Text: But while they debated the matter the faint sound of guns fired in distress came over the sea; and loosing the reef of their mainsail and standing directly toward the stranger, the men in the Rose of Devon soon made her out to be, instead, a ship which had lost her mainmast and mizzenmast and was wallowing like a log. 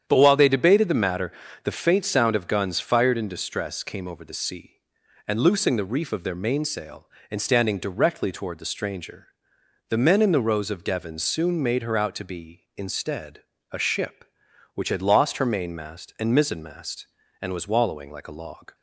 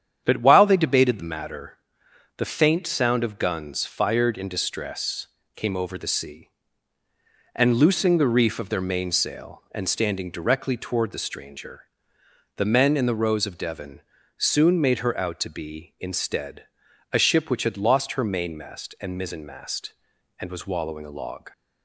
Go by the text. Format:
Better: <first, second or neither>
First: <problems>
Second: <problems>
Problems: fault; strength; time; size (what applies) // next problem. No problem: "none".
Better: first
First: starts louder than the rest; strong; until 1.0 s; 9 dB // pauses between "matter" and "the"; slight; at 1.3 s; 0.32 s long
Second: starts louder than the rest; strong; until 1.2 s; 9 dB // pauses between "matter" and "the"; noticeable; at 1.7 s; 0.60 s long // pauses between "distress" and "came"; slight; at 5.2 s; 0.28 s long // pauses between "Devon" and "soon"; slight; at 14.0 s; 0.36 s long // skips "like"; at 21.0 s